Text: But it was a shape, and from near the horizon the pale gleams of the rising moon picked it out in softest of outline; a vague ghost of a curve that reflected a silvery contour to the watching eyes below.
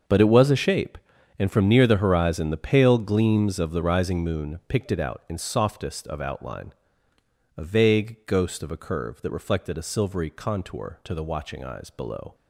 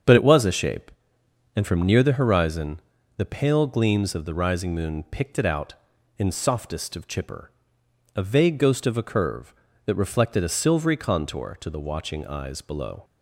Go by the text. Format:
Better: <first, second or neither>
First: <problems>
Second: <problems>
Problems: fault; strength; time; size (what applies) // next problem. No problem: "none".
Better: first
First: starts louder than the rest; until 1.4 s; 6.5 dB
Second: starts louder than the rest; strong; until 1.7 s; 7 dB // pauses between "horizon" and "the"; at 2.8 s; 0.38 s long // says "chipper" for "outline"; at 7.0 s